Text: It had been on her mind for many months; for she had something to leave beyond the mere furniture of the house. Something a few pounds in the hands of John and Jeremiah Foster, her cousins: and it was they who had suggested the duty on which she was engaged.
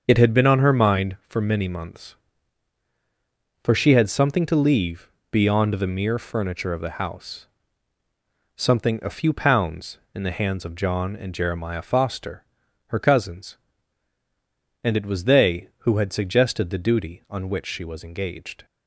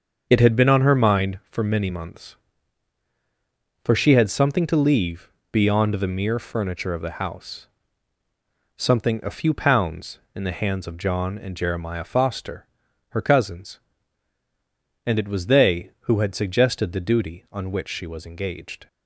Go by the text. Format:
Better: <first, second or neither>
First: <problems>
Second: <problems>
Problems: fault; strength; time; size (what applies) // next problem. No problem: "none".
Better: neither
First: starts louder than the rest; until 1.0 s; 6.5 dB // pauses between "leave" and "beyond"; slight; at 5.0 s; 0.22 s long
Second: starts louder than the rest; until 1.3 s; 6.5 dB // pauses between "leave" and "beyond"; slight; at 5.2 s; 0.22 s long